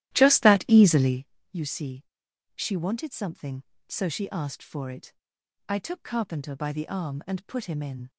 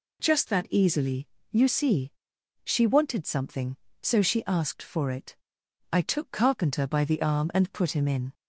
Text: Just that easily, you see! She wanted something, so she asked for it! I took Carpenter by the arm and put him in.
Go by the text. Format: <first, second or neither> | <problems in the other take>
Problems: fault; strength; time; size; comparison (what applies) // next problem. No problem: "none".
second | starts louder than the rest; strong; until 1.2 s; 14 dB